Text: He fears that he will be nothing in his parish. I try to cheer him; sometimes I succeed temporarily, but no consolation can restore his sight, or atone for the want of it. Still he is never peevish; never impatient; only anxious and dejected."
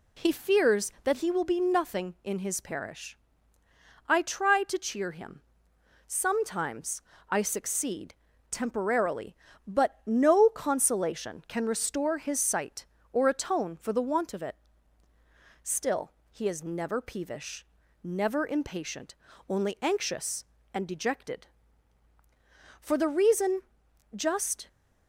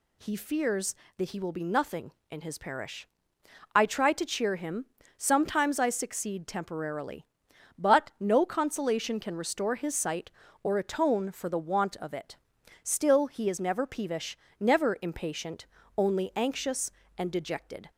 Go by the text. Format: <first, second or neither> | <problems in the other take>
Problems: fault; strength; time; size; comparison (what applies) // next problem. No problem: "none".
second | pauses between "sometimes" and "I"; slight; at 7.0 s; 0.28 s long // pauses between "succeed" and "temporarily"; slight; at 8.1 s; 0.34 s long // pauses between "Still" and "he"; slight; at 16.0 s; 0.22 s long // goes on to say "For the reason just"; strong; from 22.8 s on; 1.8 s long